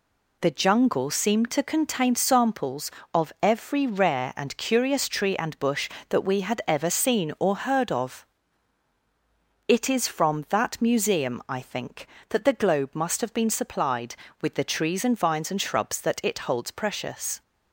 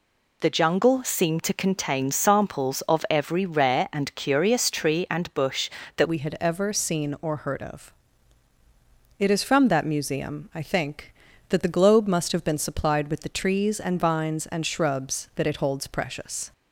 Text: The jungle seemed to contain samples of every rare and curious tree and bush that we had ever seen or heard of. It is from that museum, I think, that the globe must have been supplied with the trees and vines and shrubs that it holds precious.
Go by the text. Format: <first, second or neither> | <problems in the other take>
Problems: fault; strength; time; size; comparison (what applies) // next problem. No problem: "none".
first | changes voice at "we"; from 6.0 s on; 10.5 s long